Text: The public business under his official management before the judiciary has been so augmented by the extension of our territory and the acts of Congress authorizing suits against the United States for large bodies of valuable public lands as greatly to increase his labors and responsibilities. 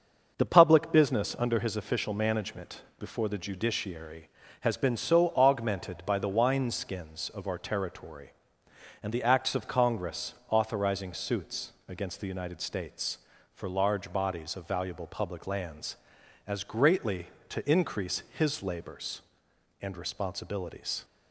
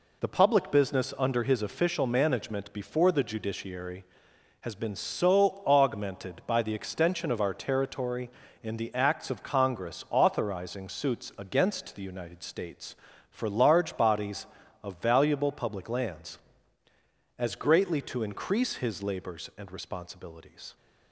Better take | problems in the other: second | starts louder than the rest; until 1.3 s; 6.5 dB // pauses between "management" and "before"; slight; at 2.8 s; 0.16 s long // says "wineskins" for "extension"; at 6.2 s // pauses between "Congress" and "authorizing"; slight; at 10.3 s; 0.16 s long // pauses between "suits" and "against"; slight; at 11.7 s; 0.16 s long

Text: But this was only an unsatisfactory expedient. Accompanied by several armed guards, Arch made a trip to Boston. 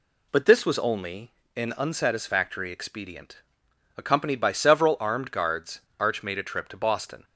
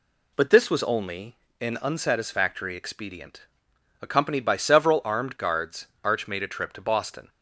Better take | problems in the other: neither | pauses between "only" and "an"; slight; the same in both

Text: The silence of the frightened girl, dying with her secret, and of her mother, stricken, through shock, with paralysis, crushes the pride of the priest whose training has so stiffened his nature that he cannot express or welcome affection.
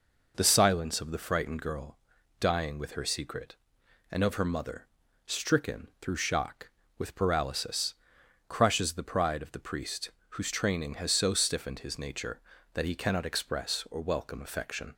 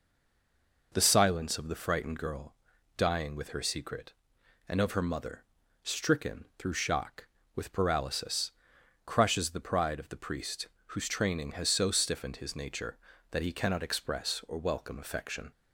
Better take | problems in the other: first | stays silent before the first word; slight; until 0.9 s; 0.9 s long // pauses between "priest" and "whose"; slight; at 10.6 s; 0.22 s long; slight in the first

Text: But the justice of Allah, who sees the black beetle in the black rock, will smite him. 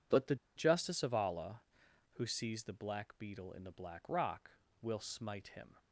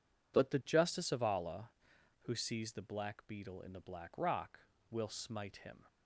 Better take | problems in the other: second | pauses between "the" and "justice"; slight; at 0.3 s; 0.20 s long

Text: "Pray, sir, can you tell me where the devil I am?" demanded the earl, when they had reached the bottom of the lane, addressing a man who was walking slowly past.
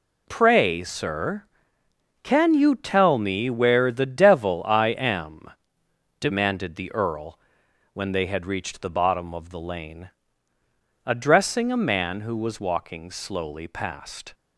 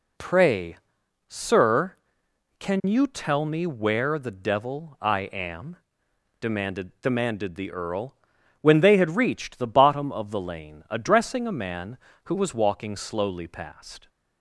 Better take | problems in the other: first | says "demanded" twice; at 7.0 s

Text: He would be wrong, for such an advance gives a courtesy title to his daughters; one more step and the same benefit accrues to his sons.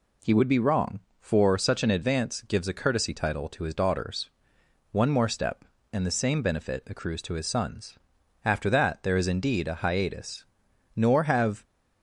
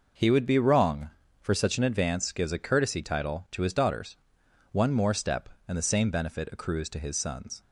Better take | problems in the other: second | goes on to say "After that there is indeed a hiatus nor have"; strong; from 8.4 s on; 3.2 s long

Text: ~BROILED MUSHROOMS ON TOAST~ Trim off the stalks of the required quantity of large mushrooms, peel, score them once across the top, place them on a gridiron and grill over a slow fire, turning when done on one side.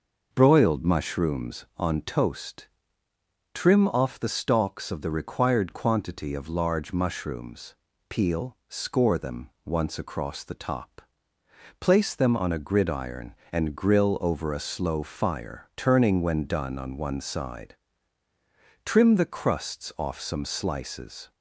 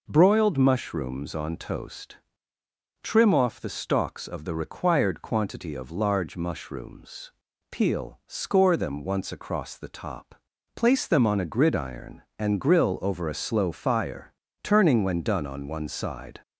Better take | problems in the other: second | pauses between "them" and "once"; slight; at 9.4 s; 0.16 s long // goes on to say "Trim the crusts off some slices"; strong; from 18.8 s on; 2.4 s long

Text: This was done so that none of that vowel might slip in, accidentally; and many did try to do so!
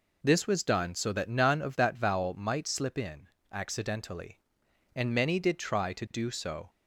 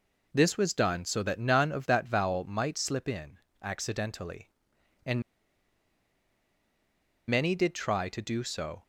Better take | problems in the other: first | pauses between "and" and "many"; strong; at 5.2 s; 2.0 s long

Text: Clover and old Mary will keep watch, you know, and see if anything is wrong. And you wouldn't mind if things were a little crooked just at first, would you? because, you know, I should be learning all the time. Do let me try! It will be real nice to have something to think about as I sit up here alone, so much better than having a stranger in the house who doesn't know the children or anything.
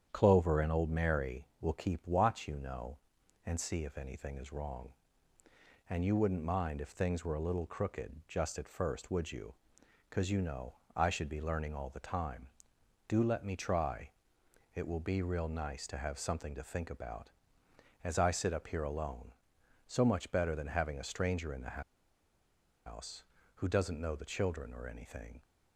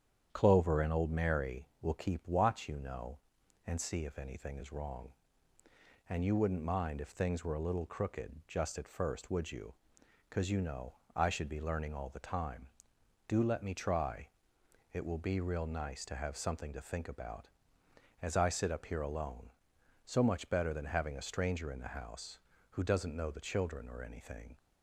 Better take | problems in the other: second | starts louder than the rest; strong; until 1.1 s; 8.5 dB; strong in the second // pauses between "the" and "house"; at 21.8 s; 1.0 s long

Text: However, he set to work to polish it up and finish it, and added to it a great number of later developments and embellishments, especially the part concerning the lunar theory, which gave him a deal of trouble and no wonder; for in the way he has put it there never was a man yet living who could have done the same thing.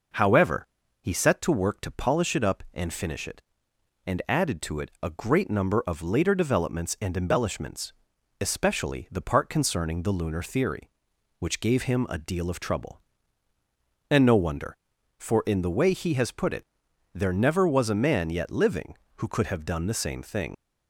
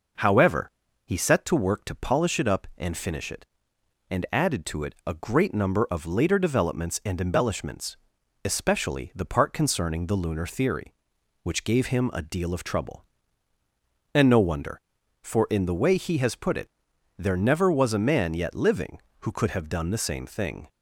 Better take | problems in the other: second | pauses between "it" and "there"; noticeable; at 16.6 s; 0.48 s long; noticeable in the second // leaves "thing" unfinished; at 20.5 s; 95 ms

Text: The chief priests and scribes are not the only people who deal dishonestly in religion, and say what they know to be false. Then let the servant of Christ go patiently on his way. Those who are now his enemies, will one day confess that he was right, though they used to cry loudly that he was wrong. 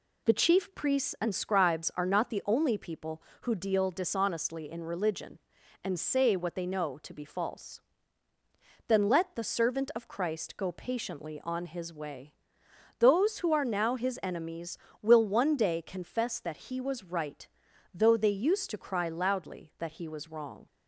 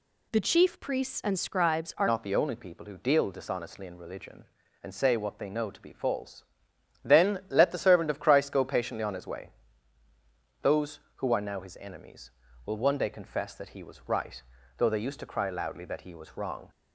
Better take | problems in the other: first | changes voice at "not"; from 2.0 s on; 14.6 s long

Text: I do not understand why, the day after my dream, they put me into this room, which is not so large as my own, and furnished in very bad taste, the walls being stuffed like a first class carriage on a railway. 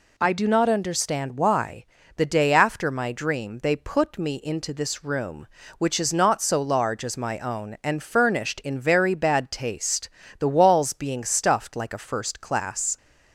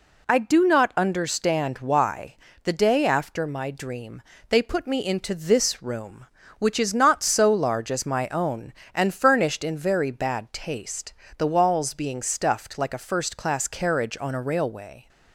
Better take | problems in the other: second | stops before "carriage on a railway"; at 12.9 s

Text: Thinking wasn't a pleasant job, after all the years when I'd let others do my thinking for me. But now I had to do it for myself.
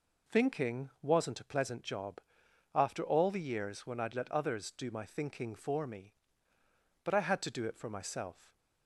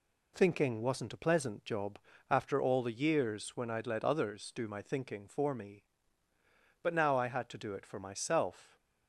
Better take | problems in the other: second | skips "now"; at 7.1 s

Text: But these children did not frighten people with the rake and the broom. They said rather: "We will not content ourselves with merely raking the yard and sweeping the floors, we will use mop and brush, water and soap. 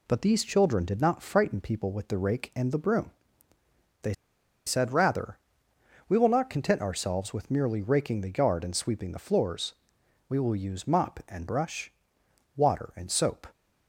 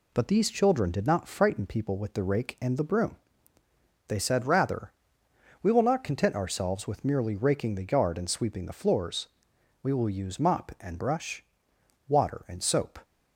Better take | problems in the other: second | pauses between "They" and "said"; noticeable; at 4.1 s; 0.54 s long

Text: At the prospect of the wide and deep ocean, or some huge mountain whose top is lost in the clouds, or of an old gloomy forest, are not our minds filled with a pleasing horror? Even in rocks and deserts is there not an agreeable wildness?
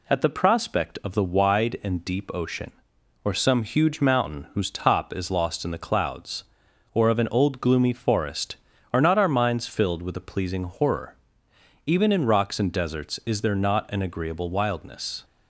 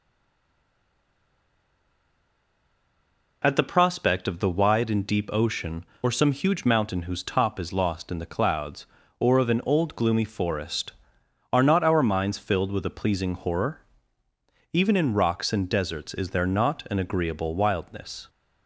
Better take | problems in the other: first | stays silent before the first word; strong; until 3.4 s; 3.4 s long

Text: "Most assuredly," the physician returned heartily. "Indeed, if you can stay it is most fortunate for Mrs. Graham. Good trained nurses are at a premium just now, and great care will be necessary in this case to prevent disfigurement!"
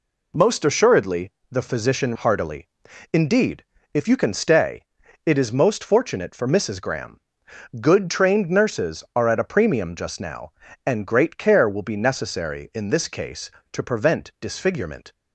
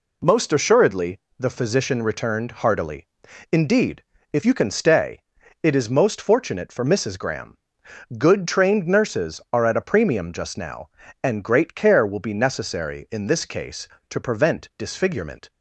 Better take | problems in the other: second | skips "returned"; at 2.1 s // pauses between "stay" and "it"; at 4.8 s; 0.42 s long; also in the second

